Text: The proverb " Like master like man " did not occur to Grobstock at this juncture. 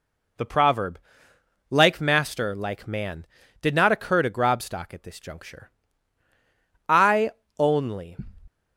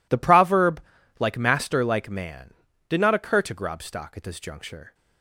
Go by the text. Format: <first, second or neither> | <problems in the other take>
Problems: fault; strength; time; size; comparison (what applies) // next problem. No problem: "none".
second | goes on to say "I only"; noticeable; from 6.8 s on; 1.2 s long